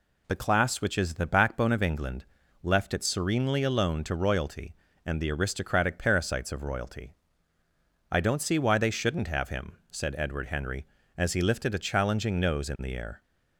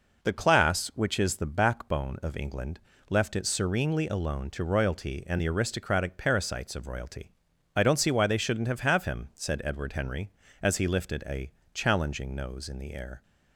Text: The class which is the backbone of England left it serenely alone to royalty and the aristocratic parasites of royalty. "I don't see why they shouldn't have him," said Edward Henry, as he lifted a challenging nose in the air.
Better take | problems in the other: first | pauses between "England" and "left"; slight; at 2.7 s; 0.30 s long; also in the first // says "have" twice; at 8.8 s // pauses between "a" and "challenging"; slight; at 11.5 s; 0.20 s long

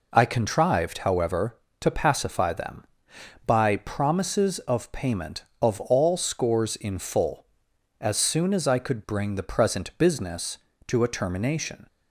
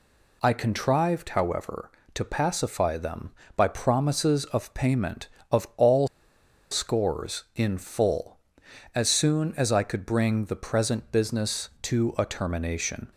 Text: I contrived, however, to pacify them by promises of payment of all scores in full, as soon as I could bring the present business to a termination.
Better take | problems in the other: first | pauses between "all" and "scores"; noticeable; at 6.0 s; 0.63 s long

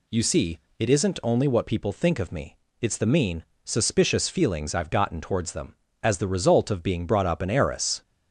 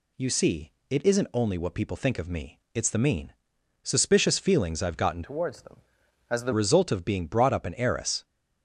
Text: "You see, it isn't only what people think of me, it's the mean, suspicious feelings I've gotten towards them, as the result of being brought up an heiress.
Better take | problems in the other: first | changes voice from "towards" to "the"; from 5.2 to 6.5 s; 1.3 s long

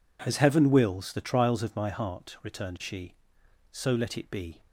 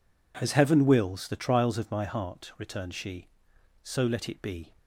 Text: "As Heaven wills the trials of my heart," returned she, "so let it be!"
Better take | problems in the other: neither | none

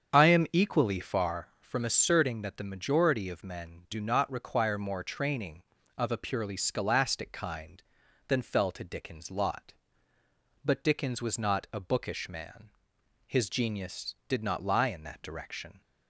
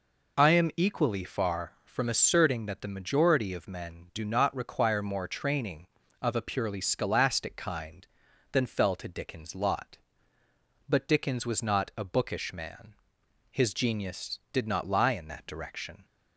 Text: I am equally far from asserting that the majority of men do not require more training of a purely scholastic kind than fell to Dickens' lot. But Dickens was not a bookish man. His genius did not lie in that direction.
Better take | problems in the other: second | starts louder than the rest; strong; until 1.4 s; 7.5 dB

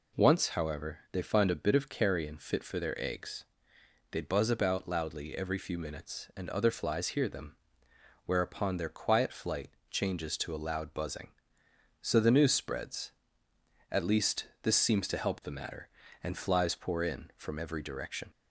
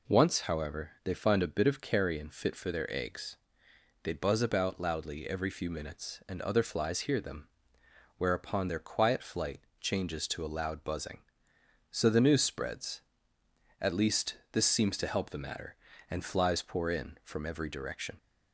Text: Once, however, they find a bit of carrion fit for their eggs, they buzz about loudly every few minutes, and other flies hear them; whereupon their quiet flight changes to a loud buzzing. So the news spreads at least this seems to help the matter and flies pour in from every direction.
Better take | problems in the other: neither | pauses between "flight" and "changes"; slight; the same in both

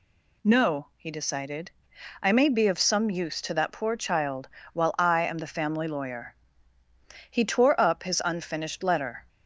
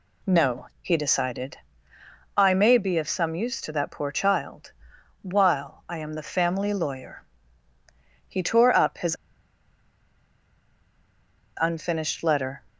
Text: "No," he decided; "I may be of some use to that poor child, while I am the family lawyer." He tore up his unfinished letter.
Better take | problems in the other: first | pauses between "his" and "unfinished"; strong; at 9.1 s; 2.4 s long

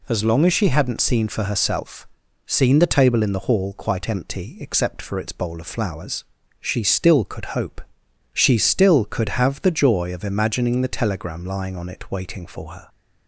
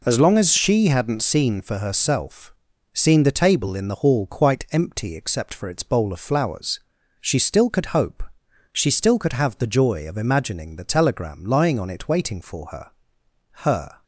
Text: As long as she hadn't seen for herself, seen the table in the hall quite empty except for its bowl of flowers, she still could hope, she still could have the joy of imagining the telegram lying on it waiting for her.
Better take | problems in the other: first | says "her" twice; at 13.6 s

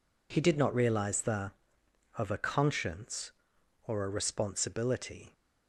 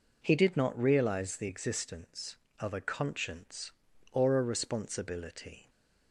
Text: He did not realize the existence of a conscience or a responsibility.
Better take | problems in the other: second | skips "existence"; at 1.8 s

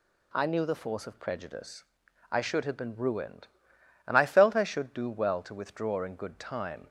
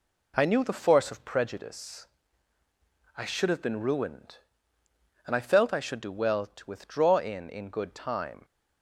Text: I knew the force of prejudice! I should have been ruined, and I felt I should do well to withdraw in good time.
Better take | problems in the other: first | says "in" twice; at 7.4 s

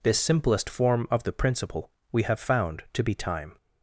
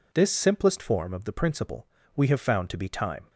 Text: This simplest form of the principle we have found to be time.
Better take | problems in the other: neither | pauses between "principle" and "we"; slight; the same in both

